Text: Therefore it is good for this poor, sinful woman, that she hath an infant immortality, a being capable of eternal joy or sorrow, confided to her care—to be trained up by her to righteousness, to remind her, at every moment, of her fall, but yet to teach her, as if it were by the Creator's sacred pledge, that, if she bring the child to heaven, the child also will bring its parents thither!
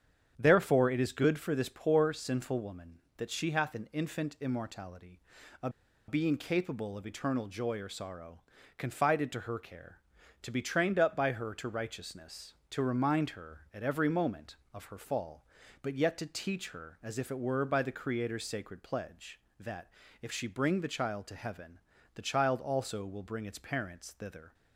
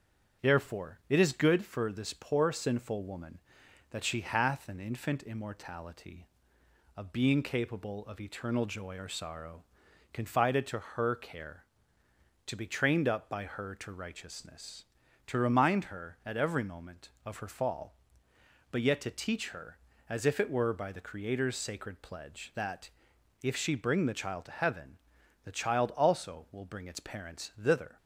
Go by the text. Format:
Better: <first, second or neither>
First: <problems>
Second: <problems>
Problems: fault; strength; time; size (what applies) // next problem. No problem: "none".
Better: second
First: starts louder than the rest; strong; until 1.3 s; 8.5 dB // pauses between "a" and "being"; at 5.6 s; 0.38 s long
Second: starts louder than the rest; strong; until 1.5 s; 7.5 dB